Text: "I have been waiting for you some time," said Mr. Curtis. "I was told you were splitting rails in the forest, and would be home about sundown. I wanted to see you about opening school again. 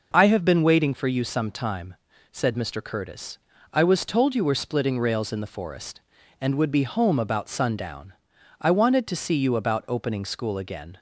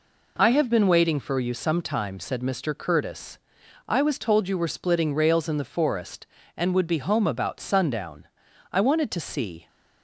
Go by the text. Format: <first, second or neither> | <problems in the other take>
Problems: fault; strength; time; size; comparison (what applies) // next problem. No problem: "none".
first | stops before "you about opening school again"; at 9.6 s